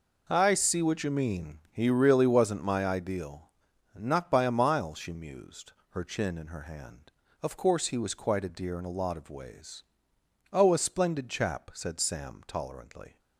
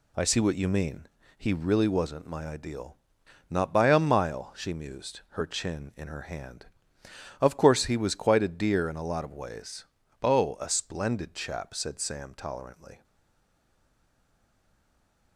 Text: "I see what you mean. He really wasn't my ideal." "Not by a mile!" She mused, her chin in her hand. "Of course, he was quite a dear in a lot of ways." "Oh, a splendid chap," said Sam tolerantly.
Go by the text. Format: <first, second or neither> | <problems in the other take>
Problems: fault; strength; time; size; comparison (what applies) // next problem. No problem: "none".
first | stays silent after the last word; from 13.0 s on; 2.3 s long